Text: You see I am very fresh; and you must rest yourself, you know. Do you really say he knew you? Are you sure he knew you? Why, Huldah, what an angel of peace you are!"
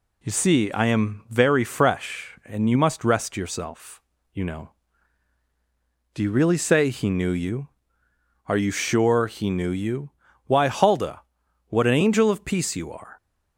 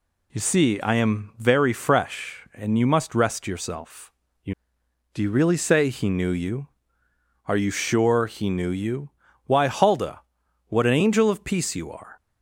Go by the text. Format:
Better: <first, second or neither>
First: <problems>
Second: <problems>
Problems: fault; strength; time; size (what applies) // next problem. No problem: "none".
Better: first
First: none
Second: skips "know"; at 4.8 s